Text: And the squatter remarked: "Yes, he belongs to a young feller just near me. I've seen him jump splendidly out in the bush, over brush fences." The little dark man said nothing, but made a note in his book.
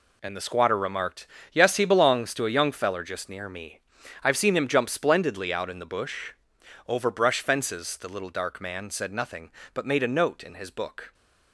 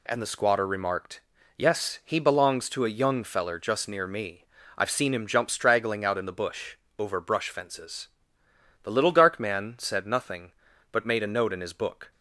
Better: first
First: none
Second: says "straggling" for "splendidly"; at 5.5 s

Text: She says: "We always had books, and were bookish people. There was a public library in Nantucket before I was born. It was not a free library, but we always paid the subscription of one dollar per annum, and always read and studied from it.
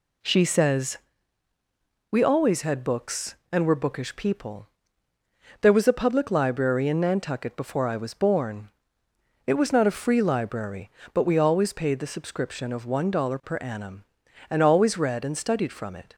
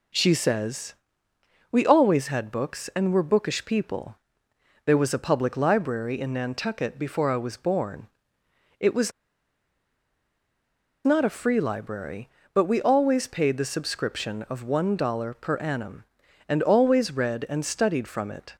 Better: first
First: none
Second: pauses between "was" and "not"; strong; at 9.1 s; 1.9 s long

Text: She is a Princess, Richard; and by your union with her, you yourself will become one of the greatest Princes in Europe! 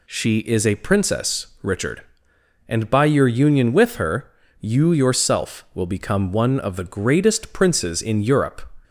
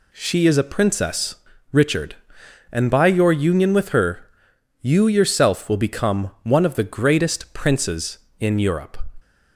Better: neither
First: none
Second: none

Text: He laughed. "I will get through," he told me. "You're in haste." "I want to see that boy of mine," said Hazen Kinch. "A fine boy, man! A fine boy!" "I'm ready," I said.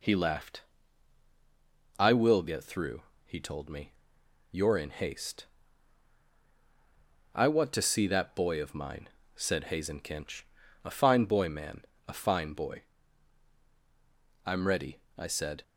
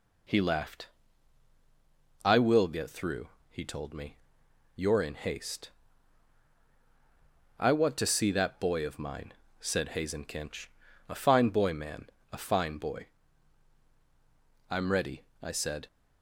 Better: neither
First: none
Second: none

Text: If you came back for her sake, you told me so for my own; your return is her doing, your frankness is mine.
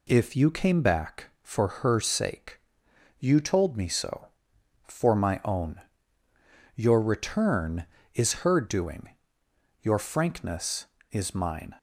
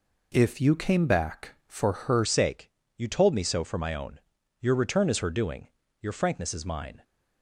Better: first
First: none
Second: changes voice at "sake"; from 2.2 s on; 4.8 s long

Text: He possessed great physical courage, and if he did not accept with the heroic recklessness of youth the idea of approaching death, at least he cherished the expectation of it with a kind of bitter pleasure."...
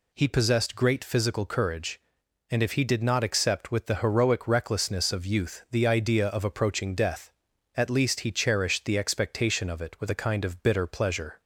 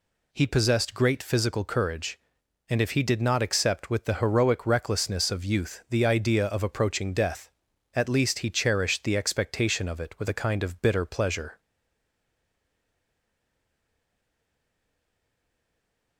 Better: first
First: none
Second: stays silent after the last word; strong; from 11.5 s on; 4.6 s long

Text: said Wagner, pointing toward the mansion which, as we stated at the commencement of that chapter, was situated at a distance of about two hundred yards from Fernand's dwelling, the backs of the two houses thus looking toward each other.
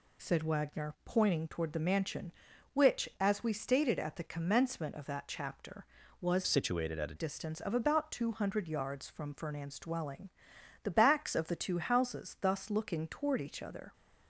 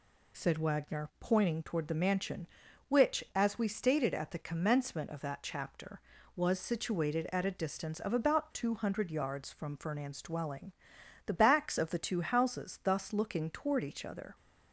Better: second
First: changes voice from "situated" to "a"; from 6.4 to 7.1 s; 0.7 s long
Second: none

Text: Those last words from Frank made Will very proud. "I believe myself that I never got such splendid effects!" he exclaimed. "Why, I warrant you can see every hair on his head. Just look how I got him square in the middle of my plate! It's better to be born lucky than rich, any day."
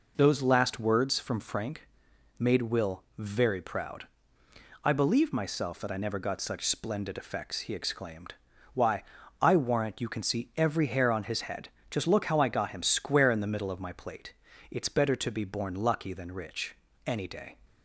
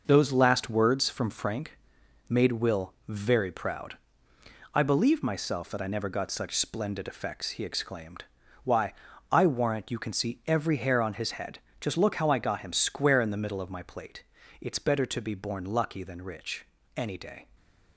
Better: first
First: pauses between "Frank" and "made"; noticeable; at 1.8 s; 0.50 s long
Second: gets quieter; throughout; 6.5 dB // pauses between "Frank" and "made"; noticeable; at 1.7 s; 0.50 s long

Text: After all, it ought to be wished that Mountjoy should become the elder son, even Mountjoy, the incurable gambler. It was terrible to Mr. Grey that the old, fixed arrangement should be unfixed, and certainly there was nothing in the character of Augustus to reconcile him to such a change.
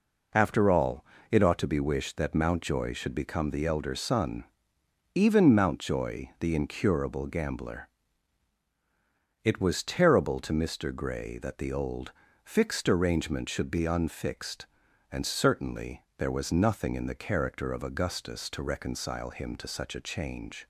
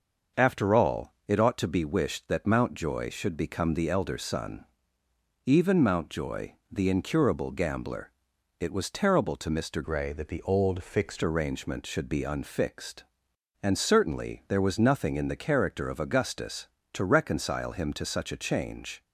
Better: first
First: none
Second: starts louder than the rest; until 1.5 s; 6 dB // changes voice from "Grey" to "fixed"; from 9.8 to 11.2 s; 1.4 s long

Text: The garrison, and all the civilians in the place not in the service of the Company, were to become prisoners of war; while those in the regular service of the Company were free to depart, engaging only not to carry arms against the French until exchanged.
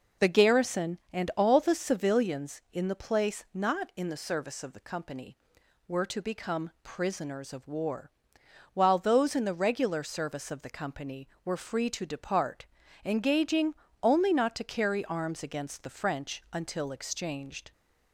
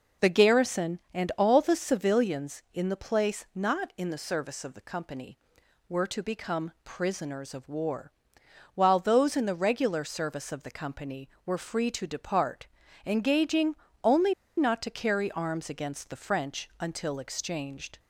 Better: first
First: pauses between "engaging" and "only"; slight; at 13.7 s; 0.28 s long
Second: pauses between "engaging" and "only"; slight; at 13.7 s; 0.28 s long // pauses between "only" and "not"; slight; at 14.3 s; 0.25 s long

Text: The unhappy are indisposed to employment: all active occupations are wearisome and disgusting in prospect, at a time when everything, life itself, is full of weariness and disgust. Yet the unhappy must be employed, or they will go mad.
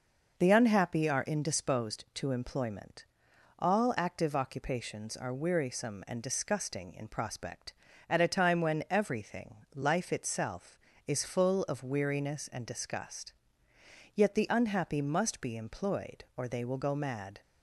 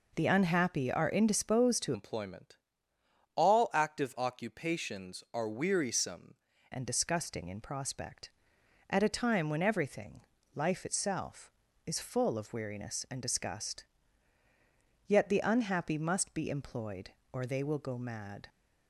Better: first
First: none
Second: changes voice from "employment" to "wearisome"; from 1.9 to 6.3 s; 4.4 s long

